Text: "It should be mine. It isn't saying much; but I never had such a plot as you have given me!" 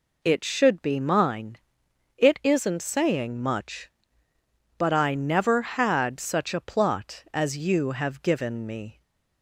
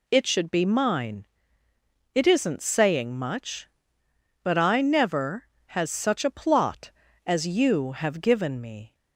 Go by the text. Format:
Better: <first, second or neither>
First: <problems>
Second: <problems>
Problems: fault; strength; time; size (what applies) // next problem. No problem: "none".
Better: first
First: none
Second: says "has" for "had"; at 5.7 s